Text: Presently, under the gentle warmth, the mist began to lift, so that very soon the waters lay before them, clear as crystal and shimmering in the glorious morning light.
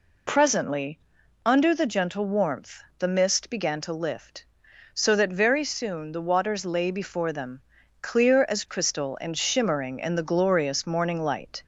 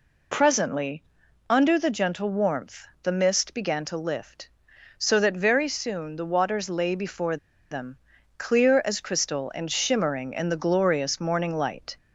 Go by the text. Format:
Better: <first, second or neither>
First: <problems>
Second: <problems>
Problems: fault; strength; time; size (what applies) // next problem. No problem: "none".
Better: first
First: none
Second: pauses between "before" and "them"; slight; at 7.3 s; 0.34 s long